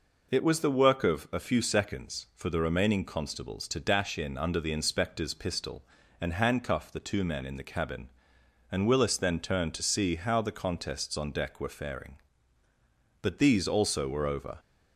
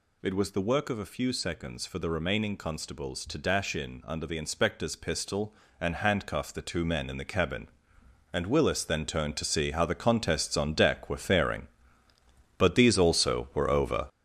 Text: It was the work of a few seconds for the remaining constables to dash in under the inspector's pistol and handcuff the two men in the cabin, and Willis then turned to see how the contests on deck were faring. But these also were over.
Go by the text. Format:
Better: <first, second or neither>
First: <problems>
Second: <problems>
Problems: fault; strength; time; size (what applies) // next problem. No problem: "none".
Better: first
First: none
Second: gets louder; strong; throughout; 8 dB